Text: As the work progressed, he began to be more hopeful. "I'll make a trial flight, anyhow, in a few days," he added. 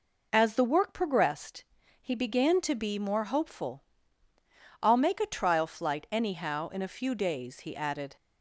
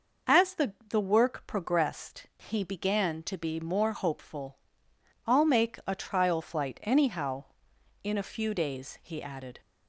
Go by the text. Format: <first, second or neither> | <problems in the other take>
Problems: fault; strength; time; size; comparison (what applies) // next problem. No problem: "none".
first | says "the" twice; at 0.9 s